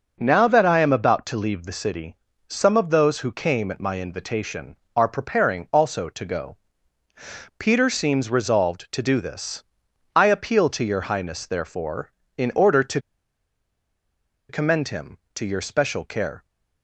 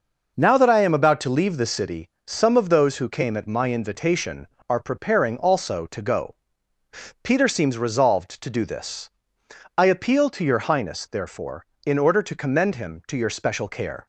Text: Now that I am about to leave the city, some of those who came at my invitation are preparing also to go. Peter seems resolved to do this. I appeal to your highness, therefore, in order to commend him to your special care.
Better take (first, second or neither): second